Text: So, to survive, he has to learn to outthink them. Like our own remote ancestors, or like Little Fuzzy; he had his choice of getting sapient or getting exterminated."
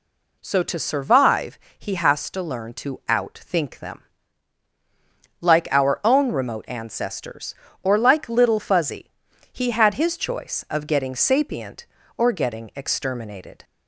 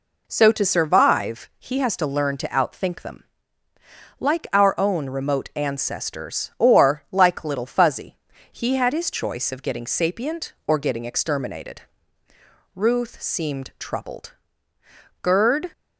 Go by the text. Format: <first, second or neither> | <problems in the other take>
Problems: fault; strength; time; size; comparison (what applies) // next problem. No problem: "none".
first | goes on to say "Ruth seemed troubled Gerd"; strong; from 12.7 s on; 2.9 s long